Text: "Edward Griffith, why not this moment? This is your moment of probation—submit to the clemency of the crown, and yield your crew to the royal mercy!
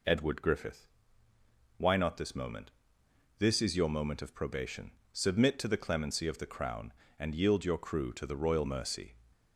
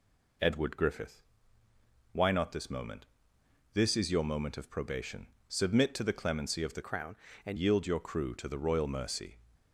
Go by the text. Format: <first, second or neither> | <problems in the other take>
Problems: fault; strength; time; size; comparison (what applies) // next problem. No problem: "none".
first | changes voice from "crown" to "and"; from 6.8 to 7.5 s; 0.7 s long